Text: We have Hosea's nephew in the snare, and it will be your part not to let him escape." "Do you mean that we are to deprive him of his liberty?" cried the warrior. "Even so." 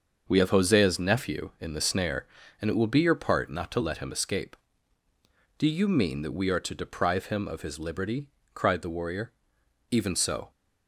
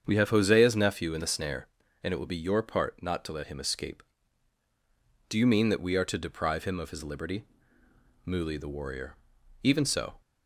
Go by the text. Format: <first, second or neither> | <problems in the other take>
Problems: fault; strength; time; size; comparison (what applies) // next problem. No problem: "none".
first | starts louder than the rest; strong; until 1.0 s; 7.5 dB; also in the first // says "muli" for "cried"; at 8.2 s